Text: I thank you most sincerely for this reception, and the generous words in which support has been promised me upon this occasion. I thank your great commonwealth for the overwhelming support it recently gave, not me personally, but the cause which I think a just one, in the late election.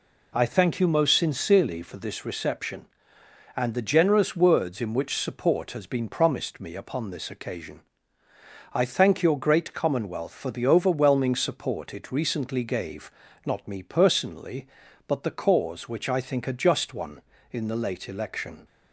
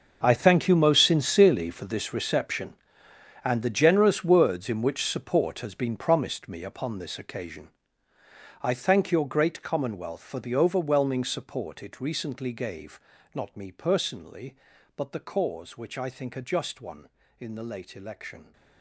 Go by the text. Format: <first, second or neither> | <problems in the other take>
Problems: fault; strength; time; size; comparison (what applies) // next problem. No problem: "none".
first | gets quieter; strong; throughout; 15.5 dB